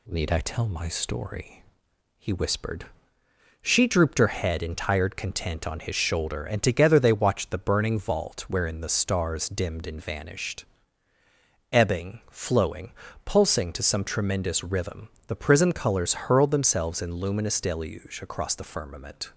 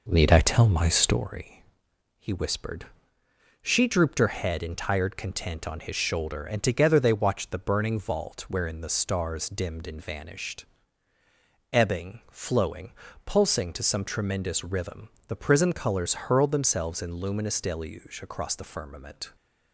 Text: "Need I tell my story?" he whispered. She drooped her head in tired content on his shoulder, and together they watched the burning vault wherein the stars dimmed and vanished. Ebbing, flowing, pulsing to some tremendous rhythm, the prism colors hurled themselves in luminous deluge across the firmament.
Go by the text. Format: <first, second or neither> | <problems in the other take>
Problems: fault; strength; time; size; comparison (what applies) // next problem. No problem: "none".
first | starts louder than the rest; noticeable; until 1.3 s; 5 dB